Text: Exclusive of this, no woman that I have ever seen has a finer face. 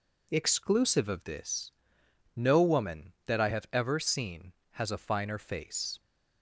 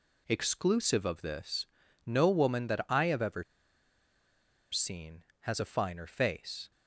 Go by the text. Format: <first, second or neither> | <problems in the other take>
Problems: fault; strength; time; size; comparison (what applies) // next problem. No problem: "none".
first | pauses between "ever" and "seen"; strong; at 3.4 s; 1.2 s long